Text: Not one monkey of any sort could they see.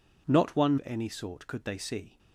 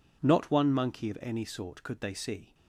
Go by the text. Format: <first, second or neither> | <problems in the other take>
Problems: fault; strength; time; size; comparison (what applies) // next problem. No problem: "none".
second | skips "monkey"; at 0.7 s